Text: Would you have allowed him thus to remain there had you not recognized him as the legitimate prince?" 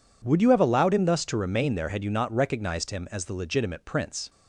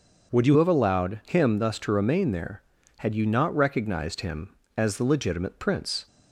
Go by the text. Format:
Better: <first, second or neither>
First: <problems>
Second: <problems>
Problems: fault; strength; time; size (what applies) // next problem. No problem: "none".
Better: first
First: none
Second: starts louder than the rest; noticeable; until 1.4 s; 6 dB // changes voice at "have"; from 0.5 s on; 5.5 s long